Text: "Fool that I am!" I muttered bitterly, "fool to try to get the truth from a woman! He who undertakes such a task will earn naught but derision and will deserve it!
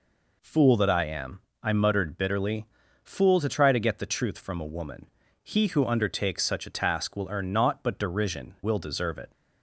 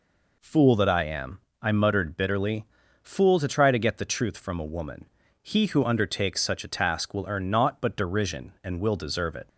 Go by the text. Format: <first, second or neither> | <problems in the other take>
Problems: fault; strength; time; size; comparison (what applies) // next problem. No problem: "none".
second | skips "and"; at 8.5 s